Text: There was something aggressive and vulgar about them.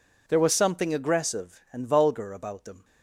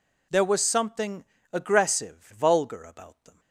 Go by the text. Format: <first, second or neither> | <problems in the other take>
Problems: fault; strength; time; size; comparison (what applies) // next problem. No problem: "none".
first | pauses between "something" and "aggressive"; slight; at 1.2 s; 0.28 s long // skips "and"; at 2.3 s